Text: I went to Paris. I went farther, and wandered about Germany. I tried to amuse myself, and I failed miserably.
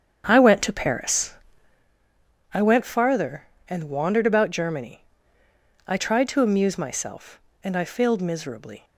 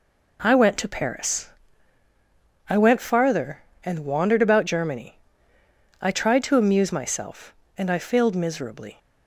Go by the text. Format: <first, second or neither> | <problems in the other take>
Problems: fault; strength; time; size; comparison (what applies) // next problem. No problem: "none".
second | starts louder than the rest; strong; until 1.9 s; 8 dB